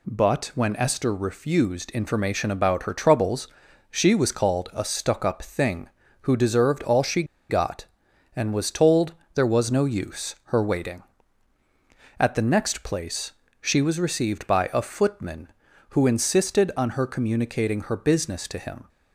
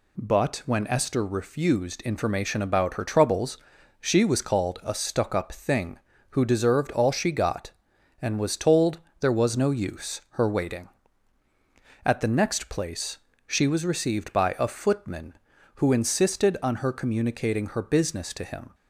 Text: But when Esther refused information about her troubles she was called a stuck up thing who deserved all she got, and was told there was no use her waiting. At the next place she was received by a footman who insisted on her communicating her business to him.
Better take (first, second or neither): second